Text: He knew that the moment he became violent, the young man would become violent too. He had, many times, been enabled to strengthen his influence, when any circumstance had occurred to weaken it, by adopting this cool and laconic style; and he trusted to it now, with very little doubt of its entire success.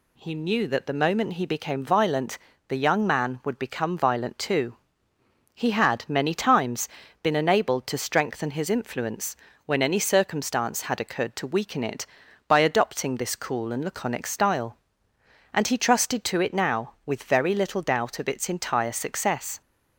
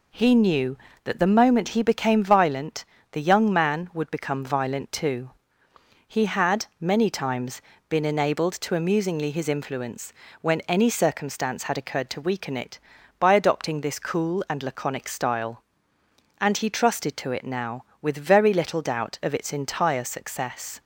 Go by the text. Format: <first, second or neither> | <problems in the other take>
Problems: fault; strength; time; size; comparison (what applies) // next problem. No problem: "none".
first | says "amusingly" for "strengthen"; at 8.7 s